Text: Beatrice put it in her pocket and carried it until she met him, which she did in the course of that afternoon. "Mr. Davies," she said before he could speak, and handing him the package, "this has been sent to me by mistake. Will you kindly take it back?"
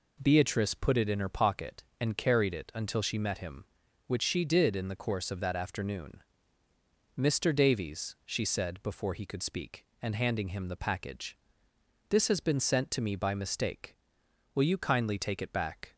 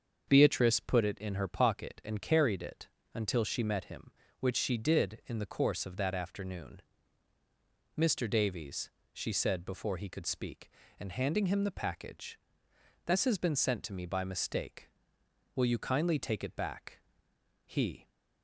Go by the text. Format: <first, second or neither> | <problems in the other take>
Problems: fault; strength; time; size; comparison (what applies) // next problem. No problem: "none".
first | starts louder than the rest; until 1.2 s; 7 dB // pauses between "it" and "until"; slight; at 2.8 s; 0.28 s long // goes on to say "He"; slight; from 17.6 s on; 0.44 s long